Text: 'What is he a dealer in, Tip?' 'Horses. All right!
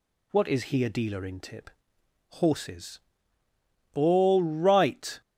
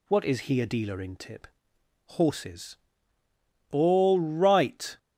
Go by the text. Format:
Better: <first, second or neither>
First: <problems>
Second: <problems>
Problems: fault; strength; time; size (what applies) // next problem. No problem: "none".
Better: neither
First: none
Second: none